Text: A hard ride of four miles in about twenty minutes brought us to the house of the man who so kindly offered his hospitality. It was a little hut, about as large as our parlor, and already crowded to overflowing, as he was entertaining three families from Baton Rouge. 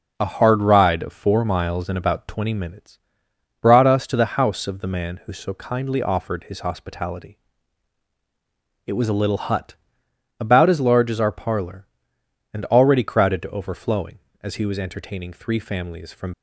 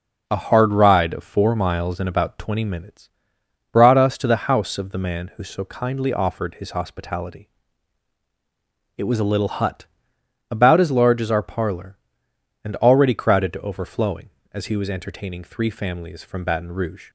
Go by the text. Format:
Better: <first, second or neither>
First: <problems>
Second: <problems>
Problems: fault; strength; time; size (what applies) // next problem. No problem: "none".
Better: second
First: pauses between "minutes" and "brought"; noticeable; at 2.9 s; 0.62 s long // stops before "Baton Rouge"; at 16.3 s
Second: pauses between "minutes" and "brought"; noticeable; at 3.0 s; 0.62 s long